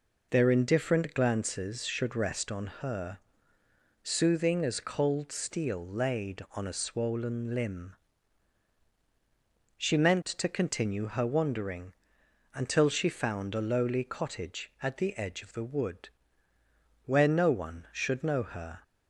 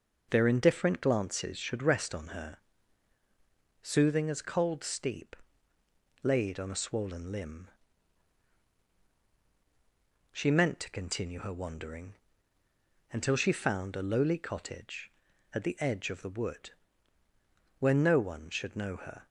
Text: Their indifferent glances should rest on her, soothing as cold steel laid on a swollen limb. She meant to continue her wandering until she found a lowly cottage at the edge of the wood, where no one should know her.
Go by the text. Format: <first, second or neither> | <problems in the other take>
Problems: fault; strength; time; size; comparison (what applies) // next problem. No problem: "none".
first | says "steep" for "steel"; at 4.8 s // pauses between "wandering" and "until"; noticeable; at 12.1 s; 0.96 s long; noticeable in the first